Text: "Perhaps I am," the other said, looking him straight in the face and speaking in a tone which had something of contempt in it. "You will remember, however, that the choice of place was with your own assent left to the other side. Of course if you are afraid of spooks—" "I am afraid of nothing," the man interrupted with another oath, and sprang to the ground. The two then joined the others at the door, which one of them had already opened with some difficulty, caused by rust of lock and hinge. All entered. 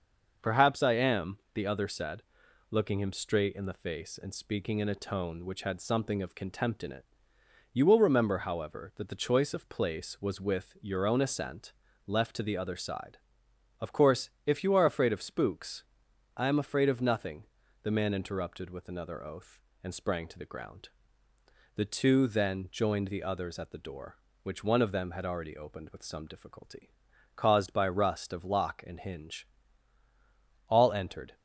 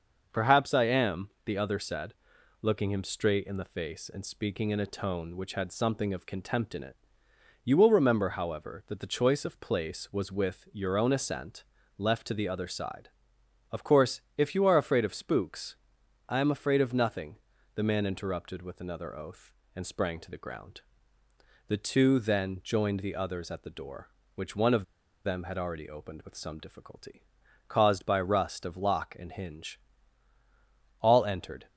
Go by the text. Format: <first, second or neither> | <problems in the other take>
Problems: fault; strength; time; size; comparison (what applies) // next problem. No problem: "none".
first | starts louder than the rest; until 1.4 s; 6.5 dB; also in the first // pauses between "assent" and "left"; slight; at 11.6 s; 0.32 s long; slight in the first // pauses between "course" and "if"; slight; at 14.2 s; 0.16 s long; slight in the first // pauses between "of" and "them"; at 24.8 s; 0.40 s long